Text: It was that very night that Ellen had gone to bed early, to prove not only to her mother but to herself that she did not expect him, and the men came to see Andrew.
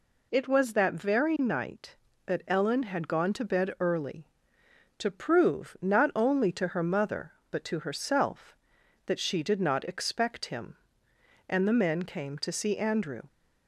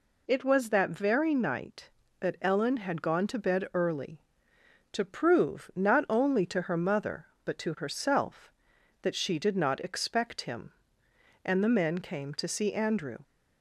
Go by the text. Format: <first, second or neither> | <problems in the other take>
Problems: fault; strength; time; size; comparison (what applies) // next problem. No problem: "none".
neither | none